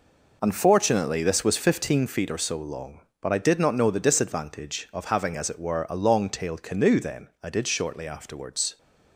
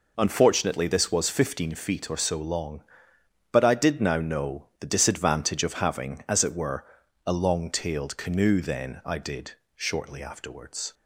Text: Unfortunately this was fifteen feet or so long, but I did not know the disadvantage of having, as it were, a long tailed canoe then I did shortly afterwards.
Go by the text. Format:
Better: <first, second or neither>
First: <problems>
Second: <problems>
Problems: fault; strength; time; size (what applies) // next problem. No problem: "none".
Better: first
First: none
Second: says "now" for "not"; at 4.0 s // pauses between "did" and "shortly"; slight; at 9.5 s; 0.22 s long